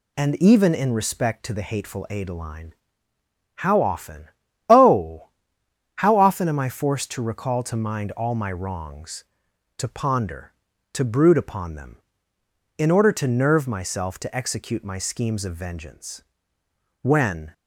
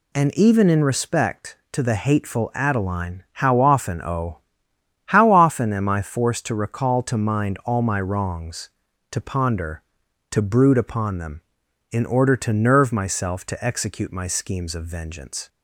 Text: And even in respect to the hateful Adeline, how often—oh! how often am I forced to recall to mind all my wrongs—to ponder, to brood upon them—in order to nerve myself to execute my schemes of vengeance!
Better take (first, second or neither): second